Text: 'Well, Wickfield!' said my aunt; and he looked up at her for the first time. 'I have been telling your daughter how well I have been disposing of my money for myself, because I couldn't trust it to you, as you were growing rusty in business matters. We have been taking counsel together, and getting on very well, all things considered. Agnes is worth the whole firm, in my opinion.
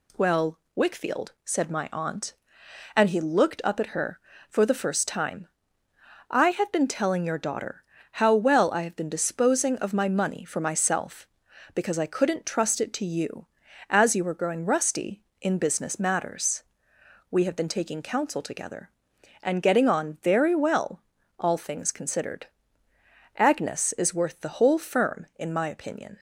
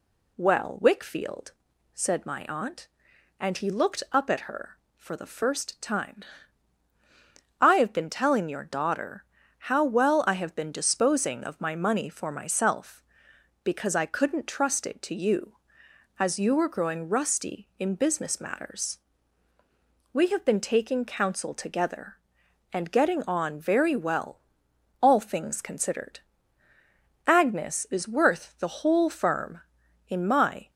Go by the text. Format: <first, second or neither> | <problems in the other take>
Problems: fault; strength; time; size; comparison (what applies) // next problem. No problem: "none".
first | pauses between "daughter" and "how"; at 9.2 s; 0.38 s long; slight in the first // pauses between "the" and "whole"; slight; at 28.6 s; 0.18 s long // stops before "opinion"; at 30.6 s